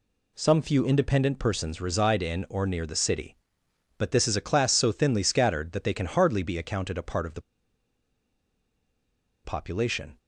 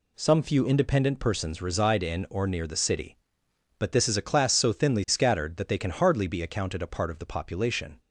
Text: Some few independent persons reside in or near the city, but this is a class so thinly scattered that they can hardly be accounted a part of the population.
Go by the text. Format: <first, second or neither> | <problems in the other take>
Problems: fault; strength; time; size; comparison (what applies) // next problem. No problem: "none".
second | pauses between "the" and "population"; strong; at 7.4 s; 2.0 s long